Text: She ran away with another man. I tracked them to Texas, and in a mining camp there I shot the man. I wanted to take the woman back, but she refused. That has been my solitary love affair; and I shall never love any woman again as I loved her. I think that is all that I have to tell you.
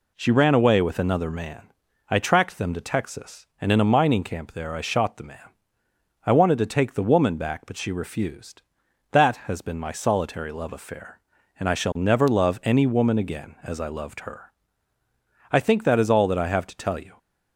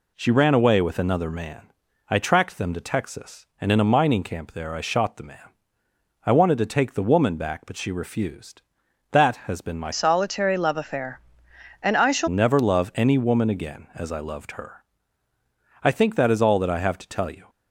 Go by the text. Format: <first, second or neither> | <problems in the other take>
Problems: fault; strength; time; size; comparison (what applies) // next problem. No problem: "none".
first | changes voice from "solitary" to "shall"; from 9.9 to 12.2 s; 2.3 s long